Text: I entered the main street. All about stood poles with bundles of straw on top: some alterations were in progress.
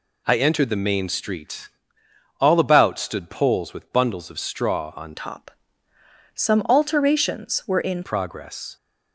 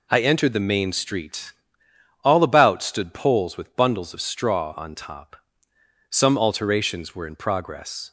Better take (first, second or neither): second